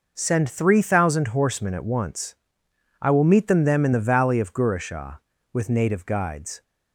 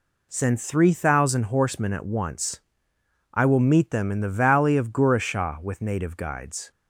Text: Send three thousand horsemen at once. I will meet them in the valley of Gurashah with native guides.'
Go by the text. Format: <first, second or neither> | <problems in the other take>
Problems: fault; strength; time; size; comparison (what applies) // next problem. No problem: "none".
second | says "them" twice; at 3.6 s